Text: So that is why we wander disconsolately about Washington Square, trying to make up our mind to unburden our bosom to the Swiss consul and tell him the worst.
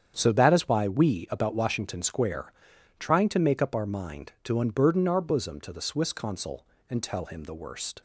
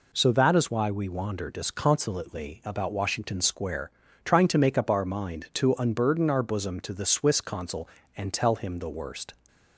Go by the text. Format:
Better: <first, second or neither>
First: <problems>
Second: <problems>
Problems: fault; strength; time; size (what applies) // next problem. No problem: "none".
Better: second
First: starts louder than the rest; strong; until 1.1 s; 8.5 dB // skips "wander disconsolately"; at 1.2 s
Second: none